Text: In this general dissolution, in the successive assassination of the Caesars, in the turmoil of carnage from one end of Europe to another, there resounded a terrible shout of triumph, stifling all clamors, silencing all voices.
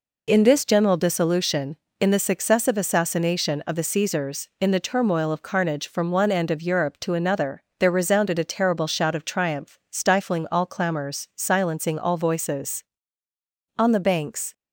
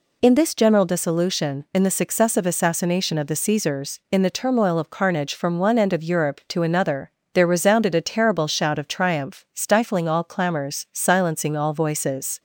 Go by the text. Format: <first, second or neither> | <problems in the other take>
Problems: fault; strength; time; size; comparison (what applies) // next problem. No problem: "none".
second | goes on to say "On the banks"; noticeable; from 13.7 s on; 0.74 s long